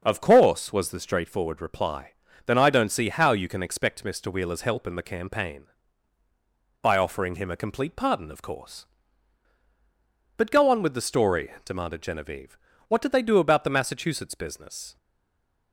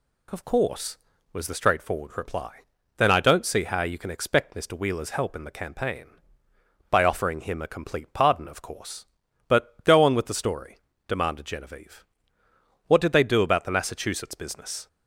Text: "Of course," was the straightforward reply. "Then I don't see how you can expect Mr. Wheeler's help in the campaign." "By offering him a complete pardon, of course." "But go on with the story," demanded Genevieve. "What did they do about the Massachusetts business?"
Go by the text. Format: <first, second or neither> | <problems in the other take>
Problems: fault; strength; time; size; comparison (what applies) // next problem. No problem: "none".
second | starts louder than the rest; until 1.0 s; 6.5 dB // stays silent after the last word; slight; from 14.9 s on; 0.8 s long